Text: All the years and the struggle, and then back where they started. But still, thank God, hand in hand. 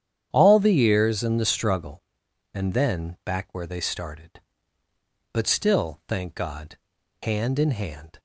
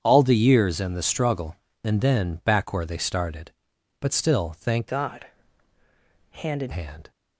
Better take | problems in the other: first | starts louder than the rest; strong; until 1.0 s; 8.5 dB; strong in the first // changes voice from "God" to "in"; from 4.8 to 6.7 s; 1.9 s long

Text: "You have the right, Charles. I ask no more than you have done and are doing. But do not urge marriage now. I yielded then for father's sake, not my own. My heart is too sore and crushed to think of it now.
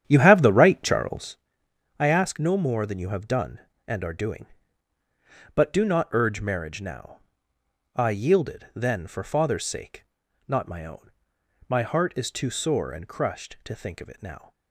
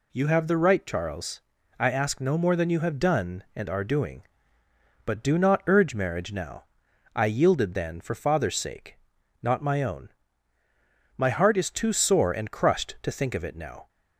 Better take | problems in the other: second | starts louder than the rest; strong; until 1.5 s; 10 dB

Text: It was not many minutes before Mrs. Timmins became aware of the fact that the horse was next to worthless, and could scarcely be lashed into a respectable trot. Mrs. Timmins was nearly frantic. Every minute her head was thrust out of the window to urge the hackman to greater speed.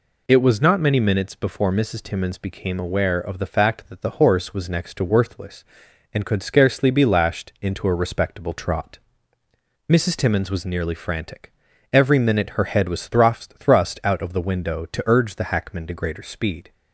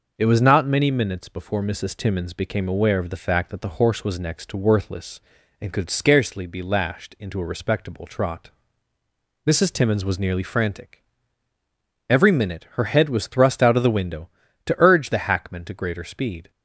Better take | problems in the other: second | says "thrust" twice; at 13.5 s

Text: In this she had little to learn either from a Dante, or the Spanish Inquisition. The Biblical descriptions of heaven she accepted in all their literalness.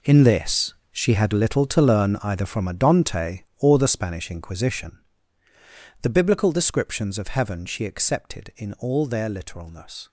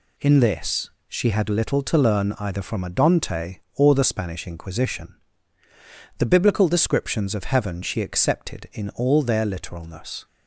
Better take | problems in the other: second | gets quieter; strong; throughout; 14.5 dB // pauses between "this" and "she"; slight; at 0.7 s; 0.18 s long; slight in the second

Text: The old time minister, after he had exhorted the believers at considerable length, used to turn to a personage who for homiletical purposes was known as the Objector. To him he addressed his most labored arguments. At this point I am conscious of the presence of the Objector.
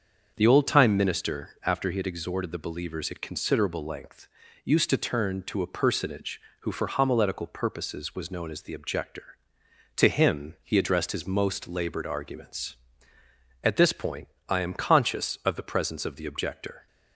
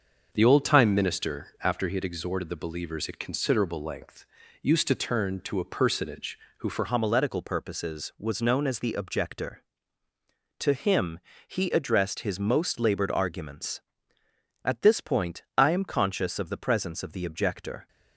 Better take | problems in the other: first | starts louder than the rest; until 1.3 s; 6.5 dB; also in the first // changes voice at "homiletical"; from 6.8 s on; 11.0 s long // pauses between "him" and "he"; slight; at 11.1 s; 0.30 s long // pauses between "point" and "I"; slight; at 15.4 s; 0.16 s long; slight in the first

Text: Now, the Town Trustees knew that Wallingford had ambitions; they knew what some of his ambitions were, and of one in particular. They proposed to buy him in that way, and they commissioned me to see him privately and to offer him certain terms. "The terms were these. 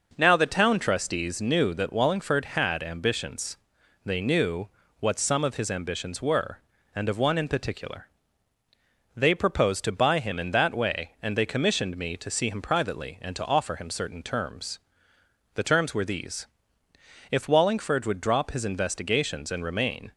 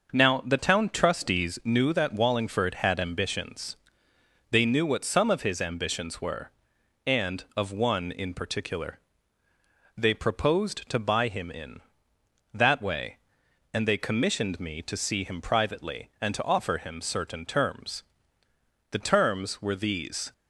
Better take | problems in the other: second | pauses between "knew" and "what"; slight; at 4.6 s; 0.32 s long // goes on to say "If Wallingford would drop his investigations and remain"; strong; from 17.3 s on; 2.8 s long

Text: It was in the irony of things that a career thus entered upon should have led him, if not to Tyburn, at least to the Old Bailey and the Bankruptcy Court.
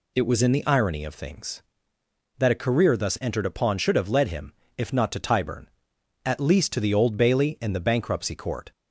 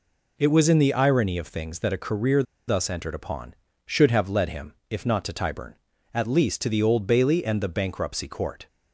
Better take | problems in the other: first | pauses between "career" and "thus"; slight; at 2.4 s; 0.25 s long

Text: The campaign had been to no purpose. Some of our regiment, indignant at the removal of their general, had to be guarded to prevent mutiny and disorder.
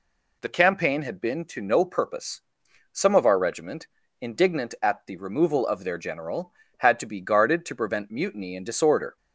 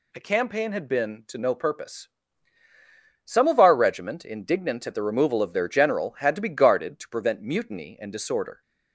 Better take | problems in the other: neither | none

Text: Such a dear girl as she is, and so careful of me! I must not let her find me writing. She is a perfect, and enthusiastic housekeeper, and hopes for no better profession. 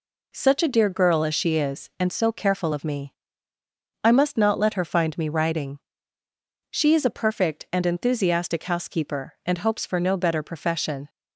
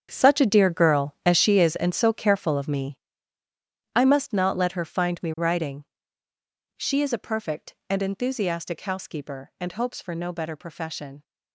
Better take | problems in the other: first | gets quieter; strong; throughout; 13 dB

